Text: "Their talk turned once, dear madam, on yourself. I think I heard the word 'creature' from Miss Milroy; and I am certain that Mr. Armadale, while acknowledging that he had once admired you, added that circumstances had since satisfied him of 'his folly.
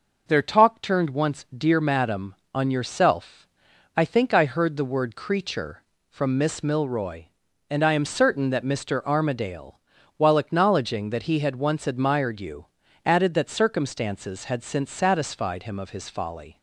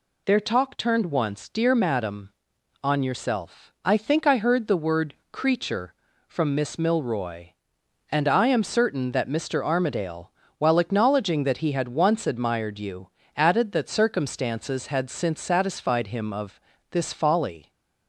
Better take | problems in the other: first | pauses between "word" and "creature"; slight; at 5.1 s; 0.18 s long // says "this" for "his"; at 16.9 s

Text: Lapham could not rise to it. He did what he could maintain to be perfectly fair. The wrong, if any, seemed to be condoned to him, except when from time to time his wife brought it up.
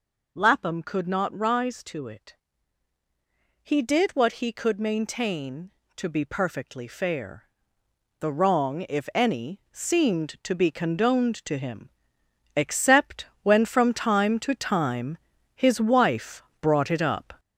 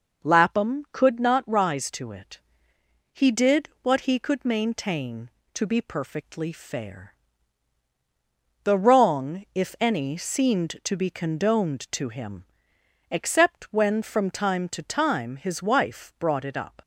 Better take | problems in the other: second | gets louder; noticeable; throughout; 5.5 dB // pauses between "except" and "when"; slight; at 13.2 s; 0.18 s long // pauses between "time" and "his"; at 15.1 s; 0.38 s long // pauses between "wife" and "brought"; slight; at 16.4 s; 0.18 s long

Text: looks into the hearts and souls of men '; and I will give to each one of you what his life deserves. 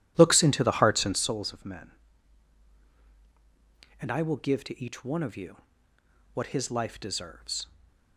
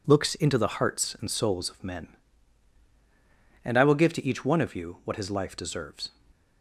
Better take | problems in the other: second | starts louder than the rest; strong; until 1.3 s; 12 dB // pauses between "you" and "what"; noticeable; at 5.5 s; 0.78 s long // stays silent after the last word; slight; from 7.6 s on; 0.5 s long

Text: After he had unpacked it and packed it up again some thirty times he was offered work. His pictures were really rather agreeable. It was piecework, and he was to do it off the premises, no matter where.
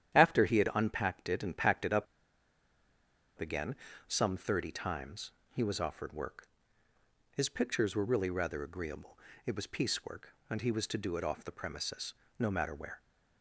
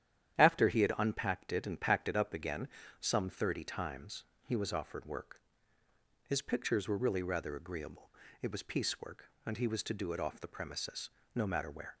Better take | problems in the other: second | starts louder than the rest; strong; until 1.1 s; 10 dB; strong in the second // pauses between "up" and "again"; strong; at 2.0 s; 1.3 s long // pauses between "again" and "some"; slight; at 3.7 s; 0.32 s long; slight in the second // pauses between "times" and "he"; slight; at 5.3 s; 0.22 s long; slight in the second

